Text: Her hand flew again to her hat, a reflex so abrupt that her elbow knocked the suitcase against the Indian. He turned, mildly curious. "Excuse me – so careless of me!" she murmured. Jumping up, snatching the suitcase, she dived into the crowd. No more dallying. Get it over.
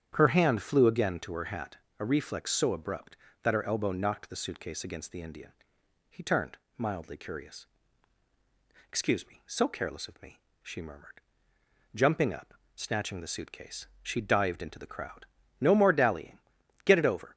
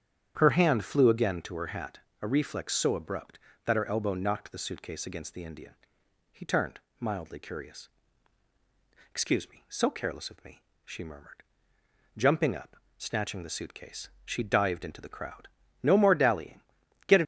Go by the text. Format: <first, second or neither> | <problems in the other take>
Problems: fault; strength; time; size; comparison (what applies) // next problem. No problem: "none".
first | starts louder than the rest; strong; until 1.3 s; 9 dB; strong in the first // stops before "over"; at 17.2 s